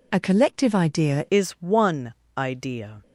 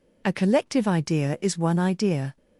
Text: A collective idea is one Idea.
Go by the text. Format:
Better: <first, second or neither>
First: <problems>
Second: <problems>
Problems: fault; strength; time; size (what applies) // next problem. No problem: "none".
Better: second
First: changes voice at "is"; from 1.2 s on; 1.8 s long // pauses between "one" and "Idea"; slight; at 2.1 s; 0.24 s long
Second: none